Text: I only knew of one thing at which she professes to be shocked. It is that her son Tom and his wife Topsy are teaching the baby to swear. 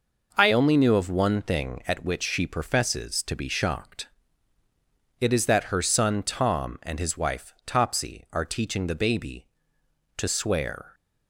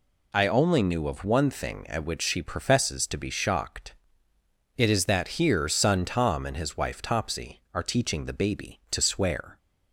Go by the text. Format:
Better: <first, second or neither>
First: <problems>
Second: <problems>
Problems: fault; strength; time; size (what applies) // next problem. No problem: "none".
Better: first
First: none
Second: says "here" for "her"; at 5.3 s